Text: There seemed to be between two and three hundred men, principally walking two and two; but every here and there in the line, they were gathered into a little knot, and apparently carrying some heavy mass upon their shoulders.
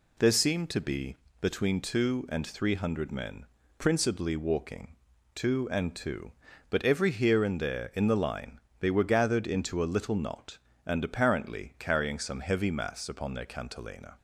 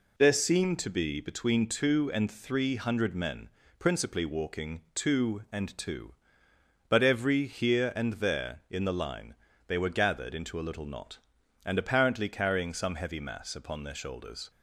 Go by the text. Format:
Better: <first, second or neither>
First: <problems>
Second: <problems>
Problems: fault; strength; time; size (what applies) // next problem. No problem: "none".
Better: second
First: pauses between "be" and "between"; slight; at 1.1 s; 0.24 s long // pauses between "walking" and "two"; at 4.9 s; 0.40 s long // says "cantilena" for "shoulders"; at 13.4 s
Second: none